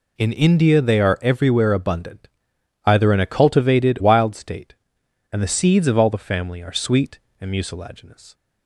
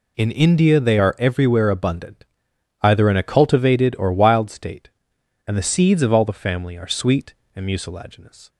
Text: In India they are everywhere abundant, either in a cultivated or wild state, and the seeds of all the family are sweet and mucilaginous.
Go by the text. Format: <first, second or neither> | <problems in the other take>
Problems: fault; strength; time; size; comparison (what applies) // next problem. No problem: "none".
second | skips "or"; at 3.9 s